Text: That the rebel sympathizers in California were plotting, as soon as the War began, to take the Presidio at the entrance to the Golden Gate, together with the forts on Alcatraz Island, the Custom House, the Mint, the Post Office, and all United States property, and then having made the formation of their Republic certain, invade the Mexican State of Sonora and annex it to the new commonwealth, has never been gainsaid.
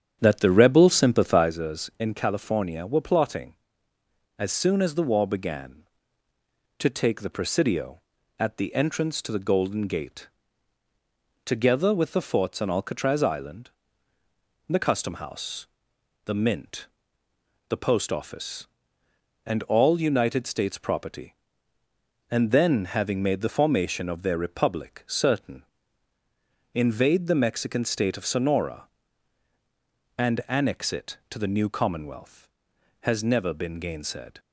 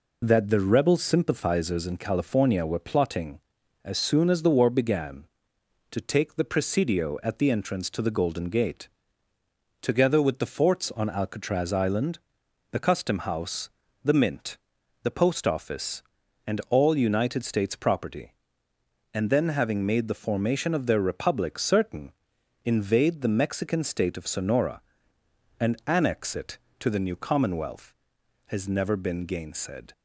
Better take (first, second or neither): second